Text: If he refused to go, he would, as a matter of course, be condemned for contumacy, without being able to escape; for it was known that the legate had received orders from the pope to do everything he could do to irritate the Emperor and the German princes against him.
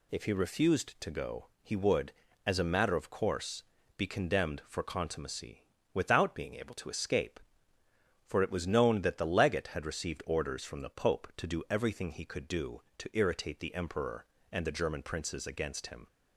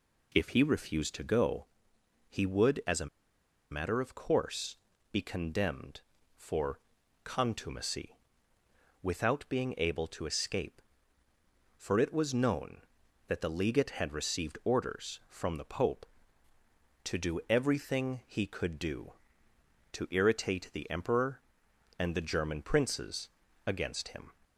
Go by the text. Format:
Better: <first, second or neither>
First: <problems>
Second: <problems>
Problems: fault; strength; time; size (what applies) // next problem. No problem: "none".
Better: first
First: none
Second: pauses between "a" and "matter"; noticeable; at 3.0 s; 0.64 s long // pauses between "for" and "contumacy"; noticeable; at 6.7 s; 0.46 s long // pauses between "princes" and "against"; at 23.2 s; 0.38 s long